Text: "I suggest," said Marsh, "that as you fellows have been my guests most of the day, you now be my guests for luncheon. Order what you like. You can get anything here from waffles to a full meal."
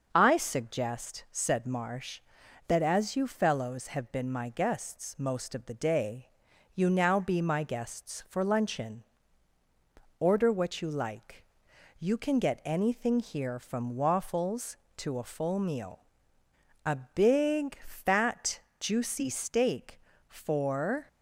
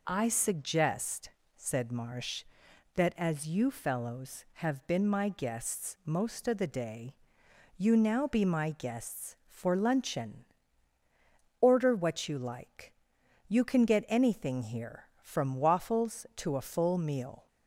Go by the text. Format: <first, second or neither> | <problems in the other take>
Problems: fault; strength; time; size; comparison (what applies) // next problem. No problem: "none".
second | starts louder than the rest; until 1.1 s; 6 dB // goes on to say "A big fat juicy steak for"; strong; from 16.8 s on; 4.2 s long